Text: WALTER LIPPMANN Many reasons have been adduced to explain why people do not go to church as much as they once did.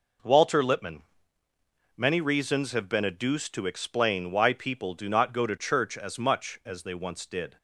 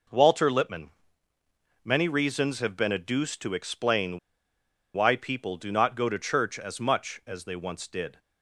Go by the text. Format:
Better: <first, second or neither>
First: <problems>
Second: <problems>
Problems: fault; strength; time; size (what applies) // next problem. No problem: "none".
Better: first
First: pauses between "LIPPMANN" and "Many"; noticeable; at 1.0 s; 0.92 s long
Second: pauses between "LIPPMANN" and "Many"; noticeable; at 0.9 s; 0.92 s long // pauses between "explain" and "why"; noticeable; at 4.1 s; 0.75 s long